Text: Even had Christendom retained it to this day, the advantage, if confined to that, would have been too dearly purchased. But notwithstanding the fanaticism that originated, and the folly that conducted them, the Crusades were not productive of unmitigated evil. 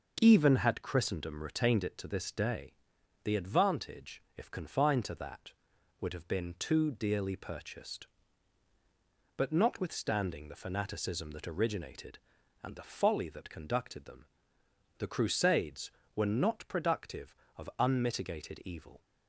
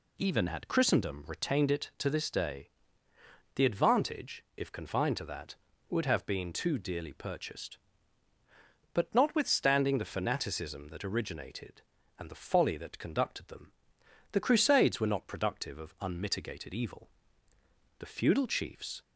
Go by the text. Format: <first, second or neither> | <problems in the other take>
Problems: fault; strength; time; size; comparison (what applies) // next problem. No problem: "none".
first | goes on to say "The feudal chiefs"; noticeable; from 17.9 s on; 1.0 s long